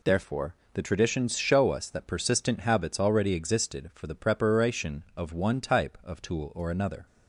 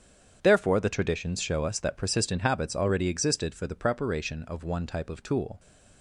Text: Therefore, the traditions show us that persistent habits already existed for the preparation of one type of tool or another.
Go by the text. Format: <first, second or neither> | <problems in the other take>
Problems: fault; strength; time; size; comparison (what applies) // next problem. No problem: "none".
first | starts louder than the rest; strong; until 1.4 s; 8 dB // stops before "or another"; at 5.5 s